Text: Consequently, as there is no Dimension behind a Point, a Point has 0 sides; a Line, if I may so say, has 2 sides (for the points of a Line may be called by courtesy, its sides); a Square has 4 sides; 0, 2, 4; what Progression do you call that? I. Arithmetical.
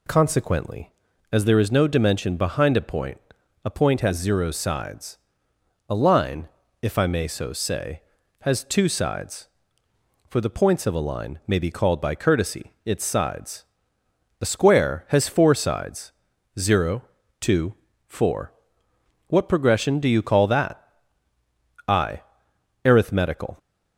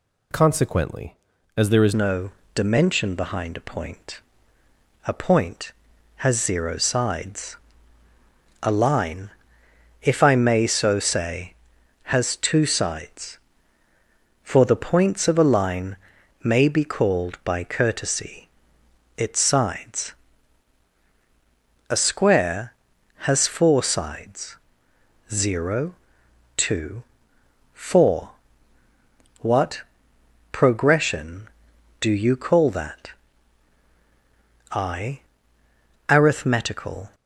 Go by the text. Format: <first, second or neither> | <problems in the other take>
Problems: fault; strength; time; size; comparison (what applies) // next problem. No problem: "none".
first | changes voice at "no"; from 1.9 s on; 35.2 s long // pauses between "no" and "Dimension"; slight; at 2.3 s; 0.24 s long // pauses between "Line" and "may"; noticeable; at 15.9 s; 0.46 s long // pauses between "what" and "Progression"; noticeable; at 29.8 s; 0.72 s long